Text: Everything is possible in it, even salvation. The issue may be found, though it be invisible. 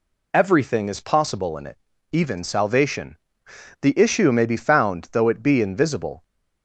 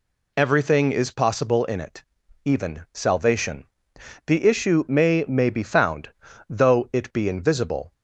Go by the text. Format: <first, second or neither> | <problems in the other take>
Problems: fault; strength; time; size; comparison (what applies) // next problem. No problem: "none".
first | says "may" twice; at 5.2 s